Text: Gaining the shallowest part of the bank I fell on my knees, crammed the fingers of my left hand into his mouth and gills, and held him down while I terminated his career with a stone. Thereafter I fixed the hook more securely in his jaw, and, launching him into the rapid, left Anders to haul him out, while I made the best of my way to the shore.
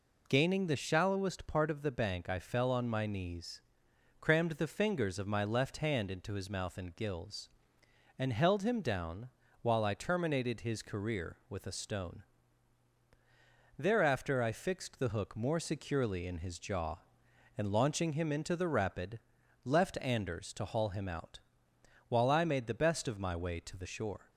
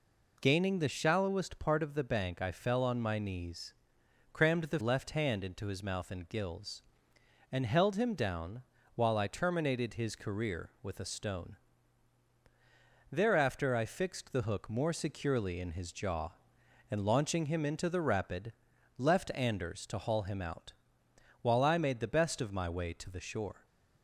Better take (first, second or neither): first